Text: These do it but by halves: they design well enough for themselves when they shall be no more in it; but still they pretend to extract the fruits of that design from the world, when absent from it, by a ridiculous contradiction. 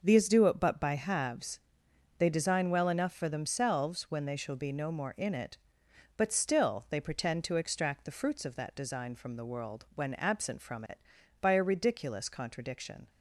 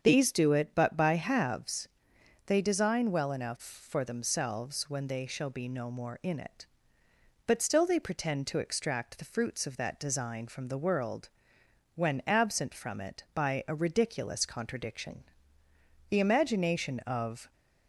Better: first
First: starts louder than the rest; noticeable; until 1.0 s; 6 dB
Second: starts louder than the rest; strong; until 1.0 s; 7.5 dB // goes on to say "The imagination of"; from 16.0 s on; 1.4 s long

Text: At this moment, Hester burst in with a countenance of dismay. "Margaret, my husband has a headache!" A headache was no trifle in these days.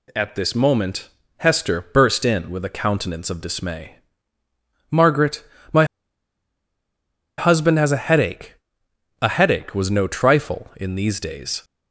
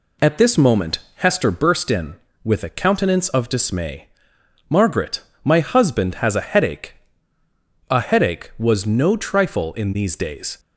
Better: second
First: pauses between "my" and "husband"; strong; at 5.8 s; 1.5 s long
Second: none

